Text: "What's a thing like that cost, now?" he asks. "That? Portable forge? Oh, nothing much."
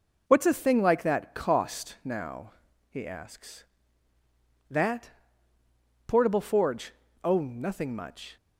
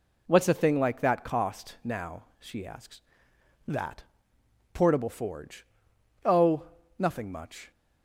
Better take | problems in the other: first | says "she" for "he"; at 2.4 s

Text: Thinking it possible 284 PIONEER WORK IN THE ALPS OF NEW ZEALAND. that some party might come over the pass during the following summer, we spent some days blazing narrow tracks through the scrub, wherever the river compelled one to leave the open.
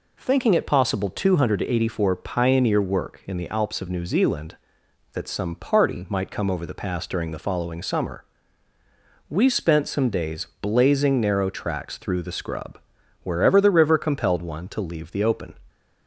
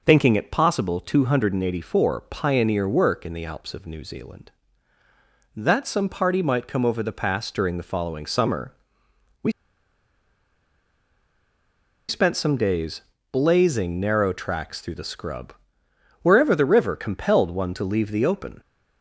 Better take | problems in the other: first | pauses between "we" and "spent"; strong; at 9.5 s; 2.5 s long // pauses between "days" and "blazing"; slight; at 12.9 s; 0.32 s long

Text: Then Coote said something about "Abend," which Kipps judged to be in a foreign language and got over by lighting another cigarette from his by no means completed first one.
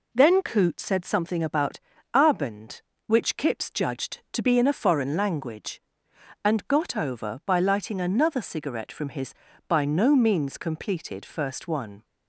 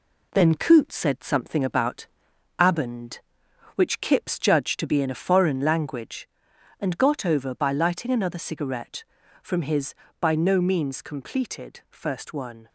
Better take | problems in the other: first | gets quieter; noticeable; throughout; 4 dB // pauses between "about" and "Abend"; noticeable; at 2.0 s; 0.54 s long; slight in the first

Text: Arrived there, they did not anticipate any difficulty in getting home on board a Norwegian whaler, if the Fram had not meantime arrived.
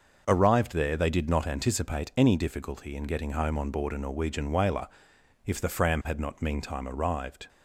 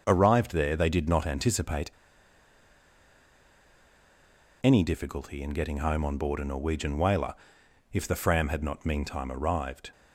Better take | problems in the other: first | starts louder than the rest; noticeable; until 1.0 s; 6 dB; noticeable in the first // pauses between "anticipate" and "any"; strong; at 1.9 s; 2.7 s long

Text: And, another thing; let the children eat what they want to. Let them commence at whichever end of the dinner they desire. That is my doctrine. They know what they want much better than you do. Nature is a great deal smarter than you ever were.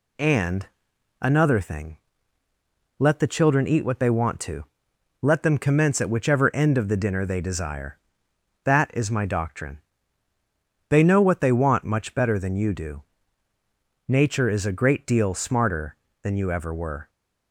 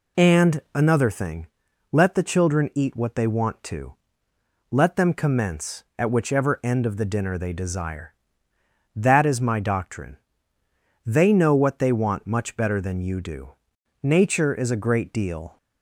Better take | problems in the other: first | stops before "smarter than you ever were"; at 15.5 s

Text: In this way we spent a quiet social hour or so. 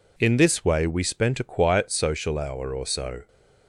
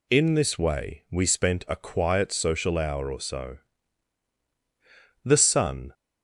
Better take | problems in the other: first | goes on to say "The sun"; noticeable; from 5.2 s on; 0.70 s long

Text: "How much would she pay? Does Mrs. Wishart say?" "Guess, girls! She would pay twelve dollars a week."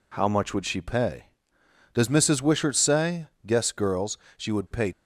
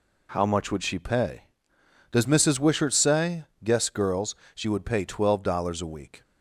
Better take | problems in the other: second | stops before "twelve dollars a week"; at 4.9 s

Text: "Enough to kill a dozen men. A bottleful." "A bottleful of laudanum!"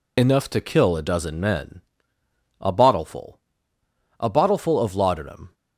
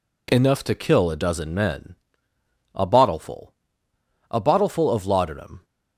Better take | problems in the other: second | loses the start of "Enough"; at 0.1 s; 45 ms

